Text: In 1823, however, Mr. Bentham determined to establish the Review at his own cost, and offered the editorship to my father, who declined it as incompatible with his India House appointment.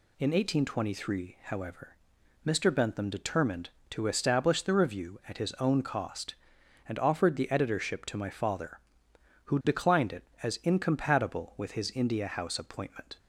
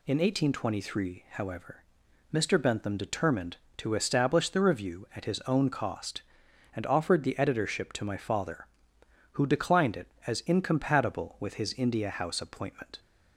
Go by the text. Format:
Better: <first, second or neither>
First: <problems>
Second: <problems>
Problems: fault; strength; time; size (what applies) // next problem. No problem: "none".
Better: neither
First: none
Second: none